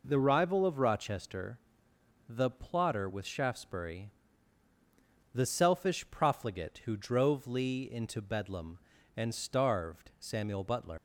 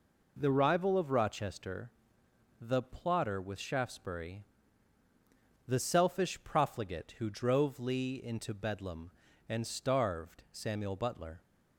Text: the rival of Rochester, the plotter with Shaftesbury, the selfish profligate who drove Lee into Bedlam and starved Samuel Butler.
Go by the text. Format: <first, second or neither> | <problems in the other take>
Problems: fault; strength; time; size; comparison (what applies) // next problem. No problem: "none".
second | leaves "Butler" unfinished; at 10.9 s; 100 ms